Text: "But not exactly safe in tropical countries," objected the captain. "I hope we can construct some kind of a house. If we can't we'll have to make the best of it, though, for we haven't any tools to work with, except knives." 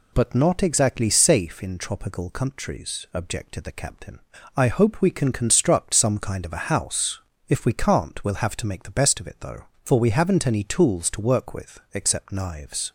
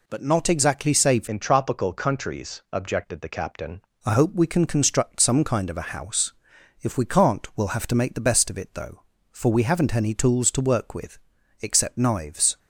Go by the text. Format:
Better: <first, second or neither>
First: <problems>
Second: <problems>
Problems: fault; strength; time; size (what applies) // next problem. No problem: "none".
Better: first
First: none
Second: changes voice from "in" to "captain"; from 1.2 to 3.8 s; 2.6 s long